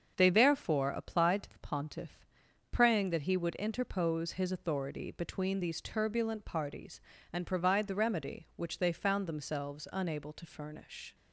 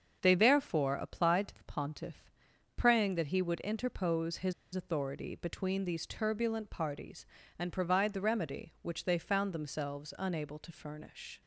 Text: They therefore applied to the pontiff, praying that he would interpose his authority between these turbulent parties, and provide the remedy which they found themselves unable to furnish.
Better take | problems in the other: first | starts louder than the rest; until 1.2 s; 7 dB; also in the first // pauses between "his" and "authority"; slight; at 4.5 s; 0.21 s long

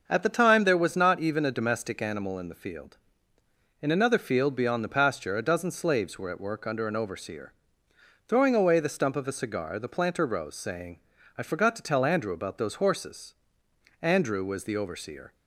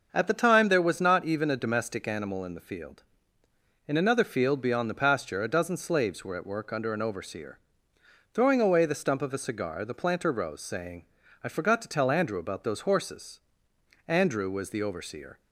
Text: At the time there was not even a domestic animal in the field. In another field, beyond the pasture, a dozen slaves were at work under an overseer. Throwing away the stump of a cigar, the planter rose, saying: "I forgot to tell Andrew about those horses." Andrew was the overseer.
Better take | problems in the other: neither | starts louder than the rest; the same in both

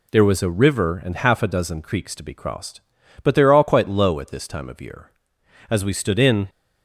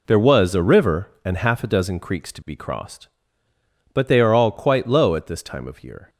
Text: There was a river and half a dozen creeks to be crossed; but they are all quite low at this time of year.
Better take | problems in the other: second | goes on to say "As we stood in"; noticeable; from 5.6 s on; 0.78 s long

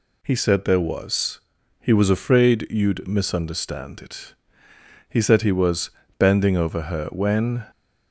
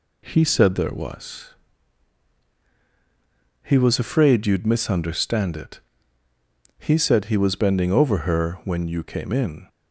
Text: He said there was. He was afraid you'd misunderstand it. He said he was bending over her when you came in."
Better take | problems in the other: second | pauses between "was" and "bending"; slight; at 5.8 s; 0.32 s long // stops before "you came in"; at 7.7 s

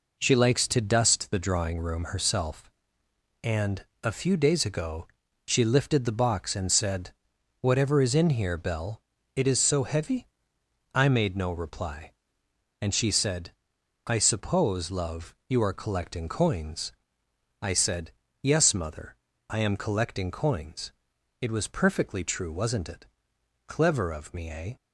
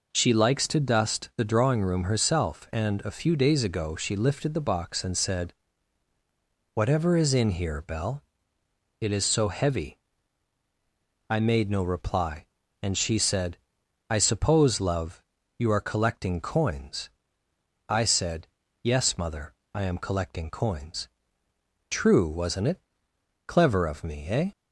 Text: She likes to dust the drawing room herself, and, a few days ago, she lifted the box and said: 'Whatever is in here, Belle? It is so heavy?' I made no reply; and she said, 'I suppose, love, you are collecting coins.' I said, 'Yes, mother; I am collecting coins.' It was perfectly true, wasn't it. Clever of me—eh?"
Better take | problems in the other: first | skips "It was perfectly"; at 21.4 s

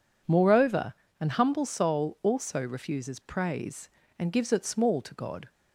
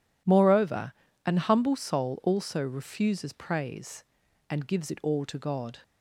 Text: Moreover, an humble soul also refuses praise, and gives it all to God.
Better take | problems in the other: second | says "small" for "all"; at 4.6 s

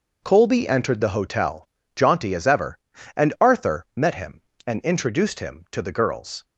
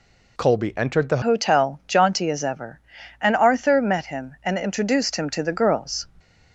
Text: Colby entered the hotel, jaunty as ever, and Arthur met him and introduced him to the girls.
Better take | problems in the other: first | changes voice at "hotel"; from 1.2 s on; 4.8 s long

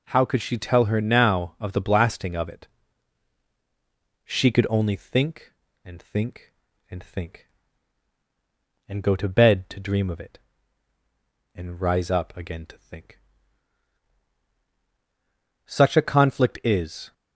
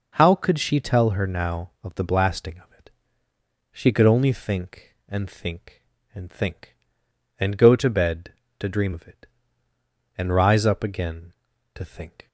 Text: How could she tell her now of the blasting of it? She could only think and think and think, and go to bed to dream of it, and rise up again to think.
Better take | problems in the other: second | goes on to say "Such a conflict is"; from 15.6 s on; 1.4 s long

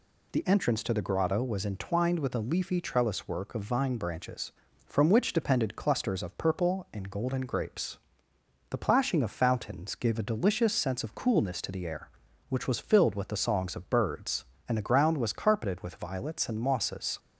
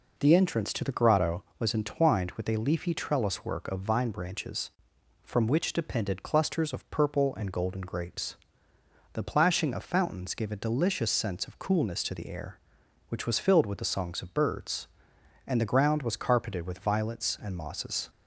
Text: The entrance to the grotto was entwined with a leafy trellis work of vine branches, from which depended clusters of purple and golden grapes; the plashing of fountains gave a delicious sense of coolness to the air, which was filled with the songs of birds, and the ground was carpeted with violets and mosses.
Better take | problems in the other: neither | none

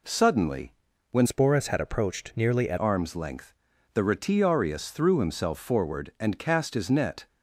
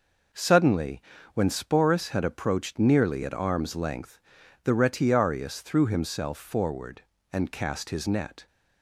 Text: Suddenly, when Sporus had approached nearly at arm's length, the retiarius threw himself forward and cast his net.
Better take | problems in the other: second | changes voice from "Sporus" to "at"; from 1.2 to 2.7 s; 1.5 s long

